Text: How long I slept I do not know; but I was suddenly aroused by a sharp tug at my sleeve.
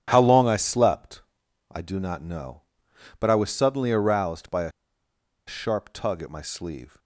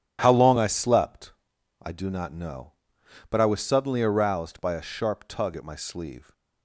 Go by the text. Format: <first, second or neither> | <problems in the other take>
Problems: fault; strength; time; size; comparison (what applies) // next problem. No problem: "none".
second | starts louder than the rest; strong; until 1.0 s; 10.5 dB // pauses between "slept" and "I"; noticeable; at 1.2 s; 0.50 s long; noticeable in the second // pauses between "a" and "sharp"; noticeable; at 4.7 s; 0.76 s long